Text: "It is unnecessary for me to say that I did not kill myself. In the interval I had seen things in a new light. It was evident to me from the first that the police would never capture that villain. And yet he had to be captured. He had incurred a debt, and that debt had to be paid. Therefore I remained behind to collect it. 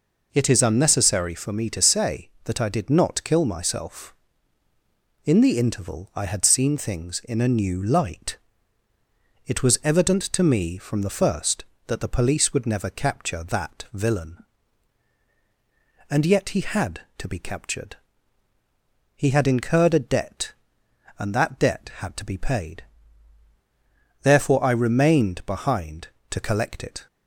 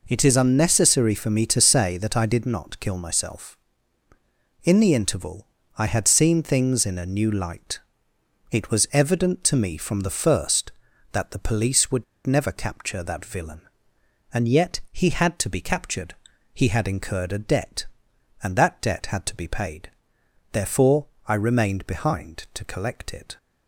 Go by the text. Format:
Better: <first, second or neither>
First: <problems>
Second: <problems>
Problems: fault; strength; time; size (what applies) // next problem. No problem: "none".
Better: first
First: none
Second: pauses between "interval" and "I"; slight; at 5.4 s; 0.32 s long // pauses between "would" and "never"; slight; at 12.0 s; 0.21 s long // pauses between "Therefore" and "I"; slight; at 21.0 s; 0.20 s long